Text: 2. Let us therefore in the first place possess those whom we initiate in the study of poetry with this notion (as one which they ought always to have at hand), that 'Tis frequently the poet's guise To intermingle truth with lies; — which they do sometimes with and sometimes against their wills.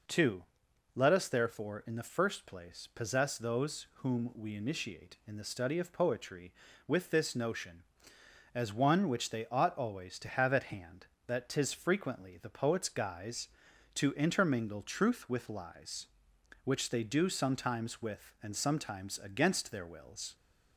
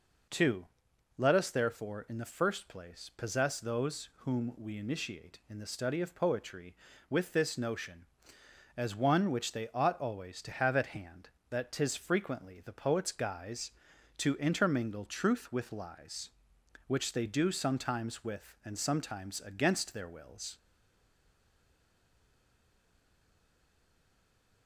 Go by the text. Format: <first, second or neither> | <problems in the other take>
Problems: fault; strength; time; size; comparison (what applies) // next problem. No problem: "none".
first | stays silent after the last word; strong; from 20.5 s on; 4.1 s long